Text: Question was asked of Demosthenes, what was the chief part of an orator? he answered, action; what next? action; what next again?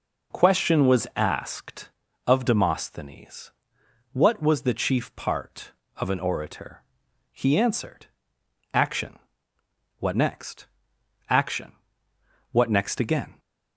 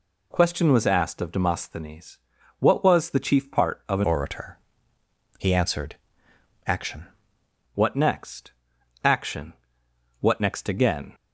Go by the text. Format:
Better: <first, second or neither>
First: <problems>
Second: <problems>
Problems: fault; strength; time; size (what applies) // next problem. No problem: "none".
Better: first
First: none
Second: changes voice from "orator" to "action"; from 4.0 to 7.0 s; 3.0 s long